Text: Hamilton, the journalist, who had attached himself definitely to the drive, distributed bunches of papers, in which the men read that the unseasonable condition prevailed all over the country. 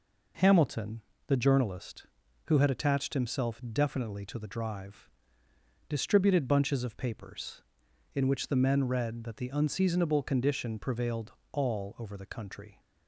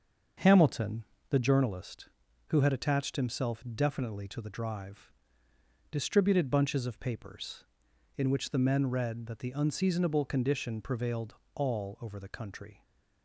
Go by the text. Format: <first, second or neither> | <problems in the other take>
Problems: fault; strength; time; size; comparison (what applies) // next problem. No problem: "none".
first | starts louder than the rest; until 1.5 s; 6.5 dB // pauses between "prevailed" and "all"; slight; at 11.3 s; 0.20 s long; slight in the first